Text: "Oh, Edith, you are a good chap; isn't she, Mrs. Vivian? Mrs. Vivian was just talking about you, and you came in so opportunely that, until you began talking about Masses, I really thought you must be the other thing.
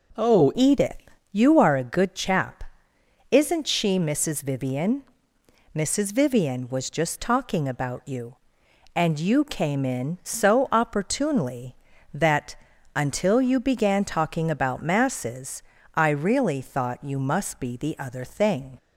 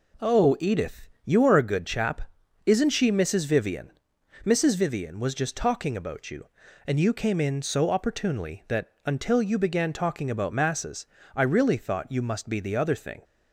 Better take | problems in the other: second | changes voice at "Edith"; from 0.5 s on; 18.2 s long

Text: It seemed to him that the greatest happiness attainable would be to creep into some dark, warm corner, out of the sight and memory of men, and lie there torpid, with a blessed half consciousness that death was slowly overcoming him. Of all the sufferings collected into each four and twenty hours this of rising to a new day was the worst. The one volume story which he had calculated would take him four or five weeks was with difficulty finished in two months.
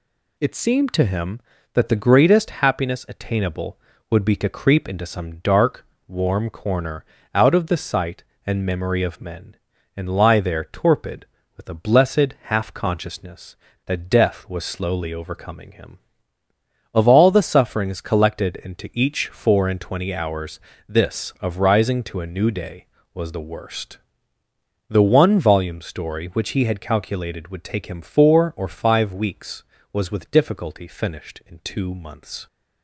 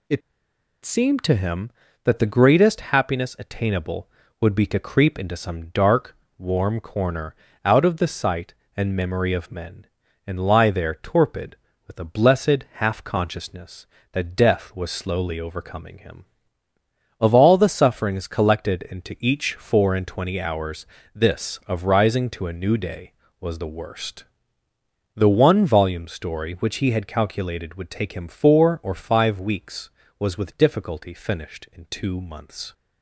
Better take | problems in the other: first | pauses between "It" and "seemed"; noticeable; at 0.2 s; 0.64 s long // pauses between "hours" and "this"; slight; at 20.8 s; 0.30 s long; slight in the first

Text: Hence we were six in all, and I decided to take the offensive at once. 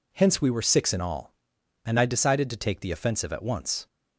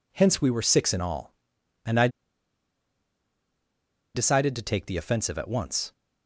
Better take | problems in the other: first | pauses between "I" and "decided"; strong; at 2.0 s; 2.0 s long

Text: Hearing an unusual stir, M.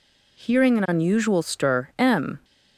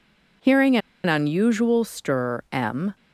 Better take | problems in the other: first | pauses between "Hearing" and "an"; slight; at 0.7 s; 0.30 s long

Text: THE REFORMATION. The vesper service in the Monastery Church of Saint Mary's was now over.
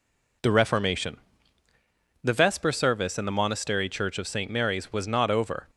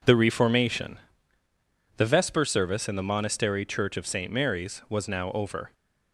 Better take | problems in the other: second | says "not" for "now"; at 5.0 s

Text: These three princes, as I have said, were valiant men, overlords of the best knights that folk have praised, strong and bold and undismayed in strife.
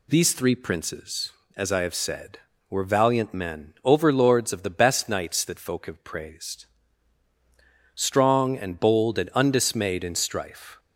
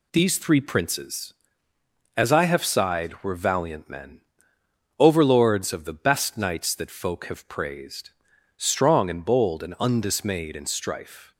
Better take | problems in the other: first | says "sighed" for "said"; at 2.6 s

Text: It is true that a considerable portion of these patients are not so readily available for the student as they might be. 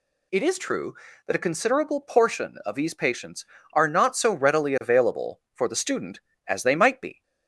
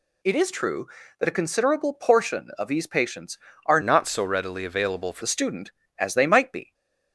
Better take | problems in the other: first | changes voice from "not" to "for"; from 3.8 to 5.2 s; 1.4 s long // stays silent after the last word; slight; from 6.6 s on; 0.5 s long

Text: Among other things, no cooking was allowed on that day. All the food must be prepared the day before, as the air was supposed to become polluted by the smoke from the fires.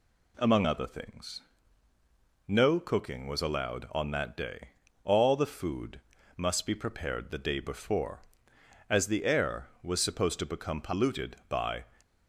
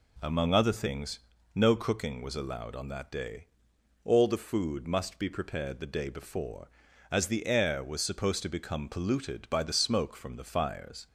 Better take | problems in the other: second | pauses between "food" and "must"; slight; at 5.9 s; 0.36 s long // stops before "the smoke from the fires"; at 12.0 s

